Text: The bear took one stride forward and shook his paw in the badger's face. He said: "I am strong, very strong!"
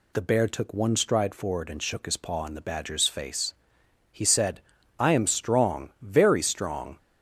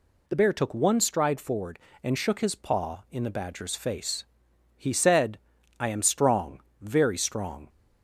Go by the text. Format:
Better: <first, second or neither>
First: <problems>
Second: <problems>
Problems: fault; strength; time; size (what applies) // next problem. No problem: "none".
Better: neither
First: none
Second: none